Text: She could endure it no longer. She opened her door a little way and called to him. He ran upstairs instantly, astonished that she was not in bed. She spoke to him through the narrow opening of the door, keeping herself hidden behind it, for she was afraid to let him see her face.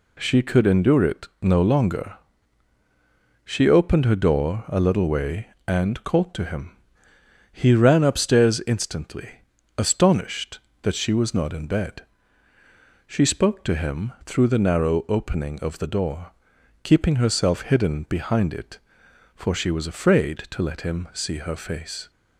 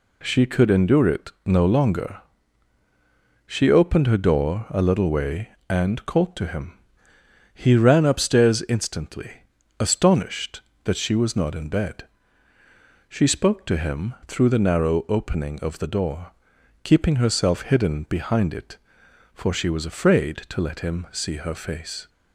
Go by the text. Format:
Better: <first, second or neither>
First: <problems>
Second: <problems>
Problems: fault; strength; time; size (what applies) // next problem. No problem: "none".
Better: neither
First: none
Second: none